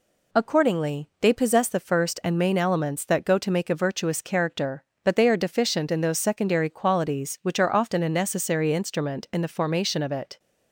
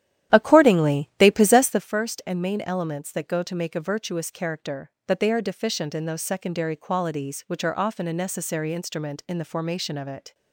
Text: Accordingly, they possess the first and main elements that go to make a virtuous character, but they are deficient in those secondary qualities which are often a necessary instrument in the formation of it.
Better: first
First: none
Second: starts louder than the rest; strong; until 1.9 s; 11.5 dB

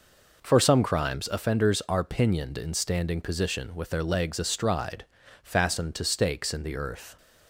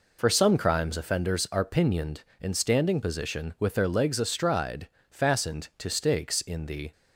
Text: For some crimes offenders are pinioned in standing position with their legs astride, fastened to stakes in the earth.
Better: first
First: none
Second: stops before "earth"; at 6.9 s

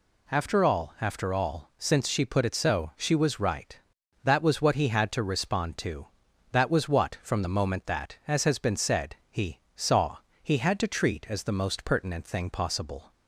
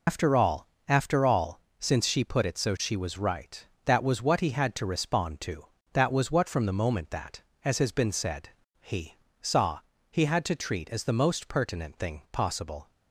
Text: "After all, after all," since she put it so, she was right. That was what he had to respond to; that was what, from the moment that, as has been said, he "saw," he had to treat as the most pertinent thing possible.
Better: first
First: pauses between "he" and "saw"; slight; at 9.6 s; 0.16 s long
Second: loses the start of "After"; at 0.0 s; 130 ms // pauses between "he" and "saw"; slight; at 9.1 s; 0.26 s long

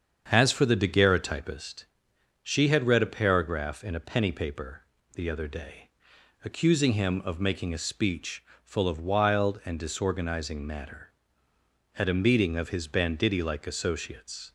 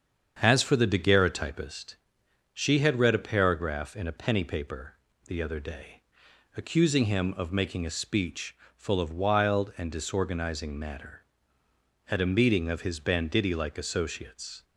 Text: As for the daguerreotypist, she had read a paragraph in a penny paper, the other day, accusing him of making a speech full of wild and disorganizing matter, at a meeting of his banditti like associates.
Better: neither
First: starts louder than the rest; strong; until 1.3 s; 7.5 dB // pauses between "speech" and "full"; slight; at 8.4 s; 0.20 s long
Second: starts louder than the rest; strong; until 1.4 s; 7.5 dB // pauses between "speech" and "full"; slight; at 8.5 s; 0.20 s long

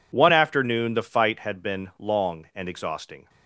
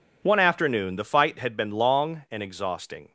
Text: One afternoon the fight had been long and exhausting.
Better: neither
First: none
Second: none

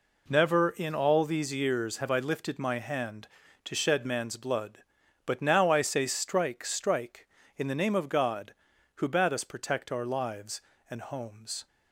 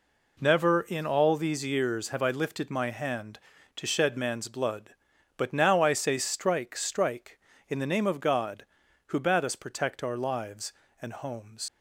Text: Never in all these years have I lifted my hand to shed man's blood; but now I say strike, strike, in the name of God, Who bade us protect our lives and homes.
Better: first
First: none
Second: leaves "homes" unfinished; at 11.6 s; 100 ms

